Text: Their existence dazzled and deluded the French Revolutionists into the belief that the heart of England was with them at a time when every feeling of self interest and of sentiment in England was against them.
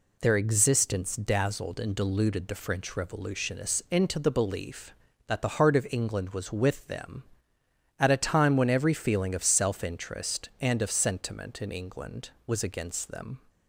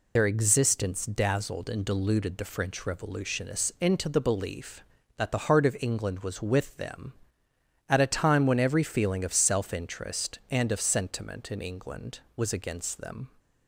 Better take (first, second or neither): first